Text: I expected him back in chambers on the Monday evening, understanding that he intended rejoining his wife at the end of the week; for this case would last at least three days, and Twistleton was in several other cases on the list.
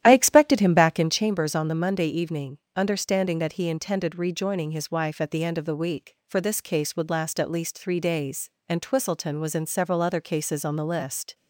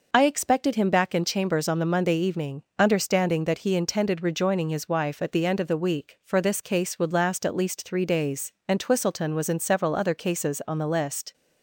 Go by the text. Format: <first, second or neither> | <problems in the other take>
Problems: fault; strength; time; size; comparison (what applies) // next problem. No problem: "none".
second | starts louder than the rest; strong; until 1.3 s; 11.5 dB